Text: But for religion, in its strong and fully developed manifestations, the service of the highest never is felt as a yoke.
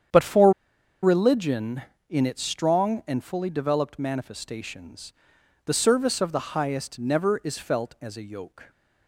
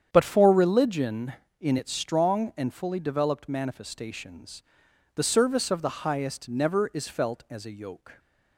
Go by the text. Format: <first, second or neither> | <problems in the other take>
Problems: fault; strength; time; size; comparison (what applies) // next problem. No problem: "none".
second | starts louder than the rest; strong; until 1.6 s; 8.5 dB; strong in the second // pauses between "for" and "religion"; noticeable; at 0.5 s; 0.52 s long